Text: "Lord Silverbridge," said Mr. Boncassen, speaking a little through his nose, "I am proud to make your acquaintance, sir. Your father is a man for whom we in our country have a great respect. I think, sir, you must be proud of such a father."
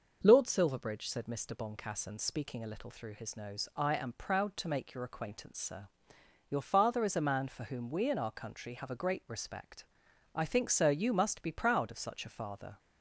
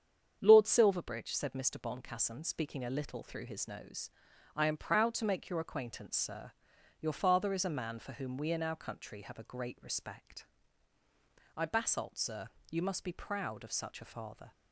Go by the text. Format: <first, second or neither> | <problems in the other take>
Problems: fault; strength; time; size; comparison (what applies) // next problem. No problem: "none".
first | starts louder than the rest; strong; until 1.4 s; 7.5 dB // says "basalt" for "think"; at 11.6 s